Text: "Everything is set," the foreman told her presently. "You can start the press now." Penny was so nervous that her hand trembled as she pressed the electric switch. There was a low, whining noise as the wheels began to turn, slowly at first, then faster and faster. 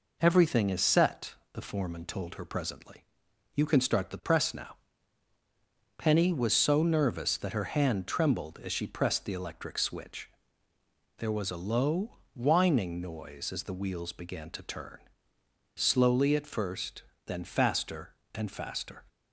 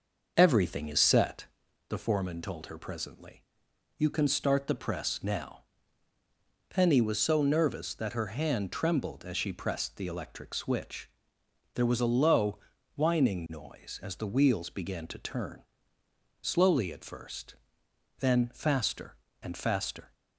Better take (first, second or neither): first